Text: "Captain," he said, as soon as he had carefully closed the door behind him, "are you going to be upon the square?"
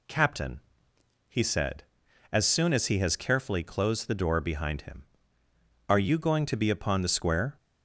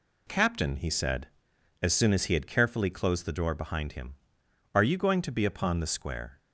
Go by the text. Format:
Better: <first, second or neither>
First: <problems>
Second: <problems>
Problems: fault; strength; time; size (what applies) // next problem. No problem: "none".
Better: second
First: says "has" for "had"; at 2.9 s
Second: none